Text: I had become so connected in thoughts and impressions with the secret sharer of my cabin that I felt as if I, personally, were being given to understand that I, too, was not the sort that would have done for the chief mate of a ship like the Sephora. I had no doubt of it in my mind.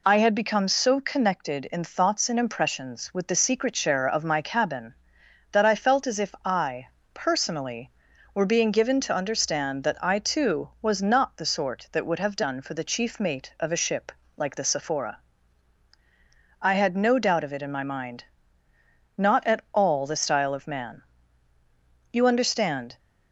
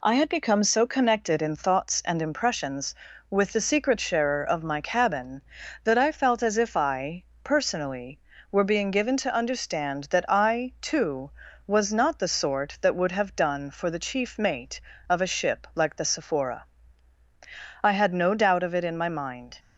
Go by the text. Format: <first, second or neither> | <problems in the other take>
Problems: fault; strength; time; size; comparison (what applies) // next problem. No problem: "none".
second | pauses between "ship" and "like"; slight; at 14.1 s; 0.24 s long // goes on to say "Not at all the style of man You understand"; strong; from 19.1 s on; 3.8 s long